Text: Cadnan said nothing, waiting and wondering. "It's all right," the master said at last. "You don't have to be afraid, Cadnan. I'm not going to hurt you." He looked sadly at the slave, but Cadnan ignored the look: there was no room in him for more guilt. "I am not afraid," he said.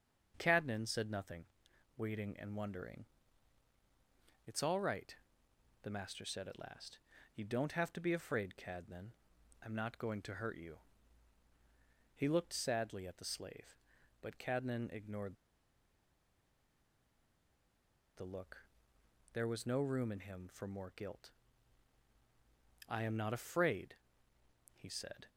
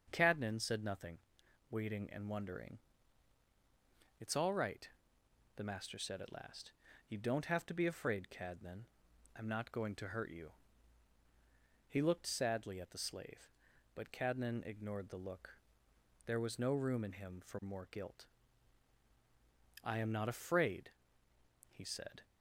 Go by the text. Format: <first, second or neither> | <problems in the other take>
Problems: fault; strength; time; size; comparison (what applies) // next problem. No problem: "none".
second | starts louder than the rest; until 1.3 s; 6.5 dB; also in the second // pauses between "ignored" and "the"; strong; at 15.3 s; 2.8 s long